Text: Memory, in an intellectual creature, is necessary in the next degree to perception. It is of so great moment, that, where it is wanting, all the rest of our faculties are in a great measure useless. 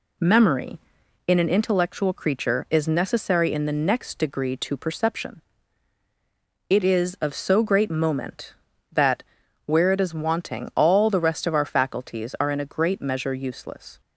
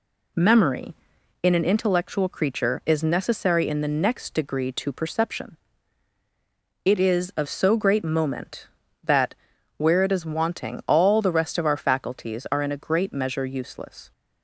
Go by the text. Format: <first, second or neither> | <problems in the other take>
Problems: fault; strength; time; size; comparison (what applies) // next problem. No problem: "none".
neither | none